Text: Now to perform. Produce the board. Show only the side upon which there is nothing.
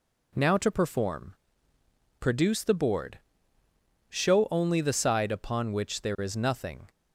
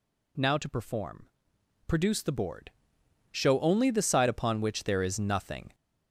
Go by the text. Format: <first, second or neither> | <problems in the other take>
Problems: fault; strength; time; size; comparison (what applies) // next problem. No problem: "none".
first | gets louder; noticeable; throughout; 4 dB